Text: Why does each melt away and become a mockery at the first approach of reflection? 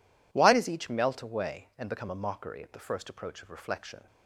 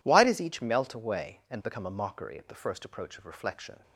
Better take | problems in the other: neither | none

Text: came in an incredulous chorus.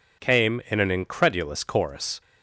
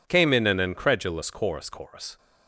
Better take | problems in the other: first | says "chorus" twice; at 1.6 s

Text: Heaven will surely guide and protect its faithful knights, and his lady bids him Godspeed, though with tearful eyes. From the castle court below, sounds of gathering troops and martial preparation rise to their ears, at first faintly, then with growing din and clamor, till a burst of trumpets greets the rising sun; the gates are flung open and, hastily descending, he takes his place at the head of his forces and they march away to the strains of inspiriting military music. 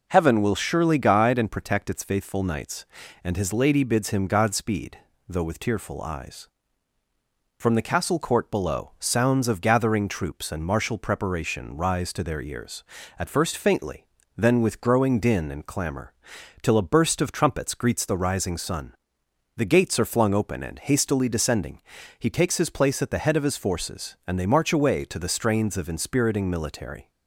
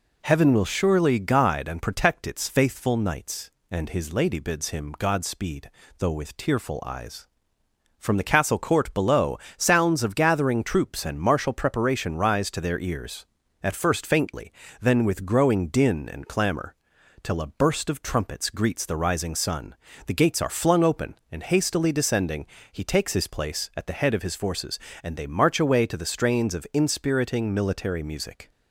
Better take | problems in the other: second | stops before "music"; at 27.0 s

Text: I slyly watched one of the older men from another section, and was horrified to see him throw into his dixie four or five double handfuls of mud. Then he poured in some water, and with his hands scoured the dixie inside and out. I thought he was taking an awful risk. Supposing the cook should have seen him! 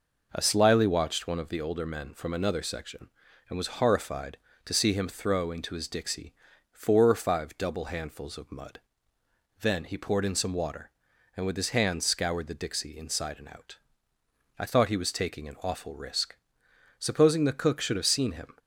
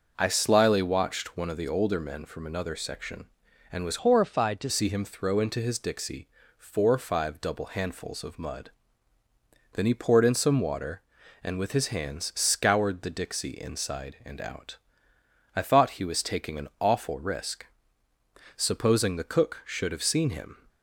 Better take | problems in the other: first | starts louder than the rest; until 1.1 s; 6 dB // changes voice from "horrified" to "to"; from 4.0 to 4.6 s; 0.6 s long // pauses between "dixie" and "four"; slight; at 6.2 s; 0.30 s long; slight in the first

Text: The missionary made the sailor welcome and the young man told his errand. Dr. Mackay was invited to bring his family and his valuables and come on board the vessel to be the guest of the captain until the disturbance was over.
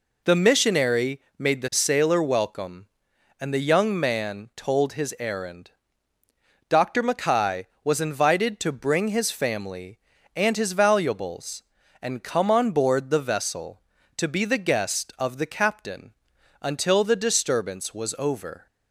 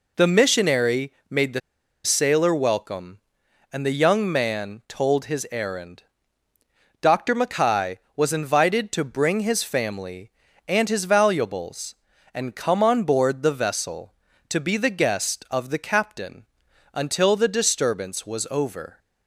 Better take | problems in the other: first | pauses between "missionary" and "made"; slight; at 1.1 s; 0.18 s long; slight in the first // pauses between "the" and "sailor"; at 1.6 s; 0.44 s long // pauses between "captain" and "until"; noticeable; at 16.4 s; 0.48 s long; noticeable in the first

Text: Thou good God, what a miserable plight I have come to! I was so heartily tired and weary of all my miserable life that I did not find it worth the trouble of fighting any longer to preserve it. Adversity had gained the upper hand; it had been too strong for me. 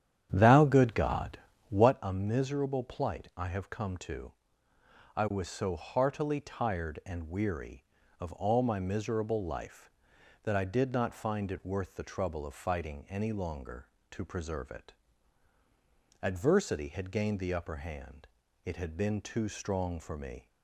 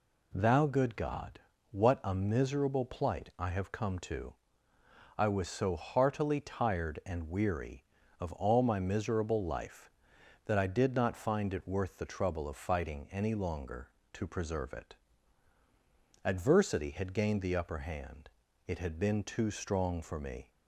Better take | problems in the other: second | starts louder than the rest; strong; until 1.9 s; 9.5 dB

